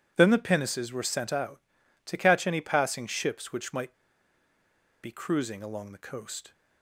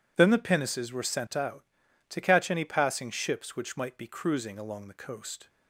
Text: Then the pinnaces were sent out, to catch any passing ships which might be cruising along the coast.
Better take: second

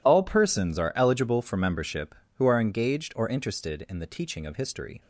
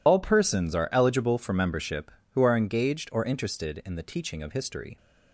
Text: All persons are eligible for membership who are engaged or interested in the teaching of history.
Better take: first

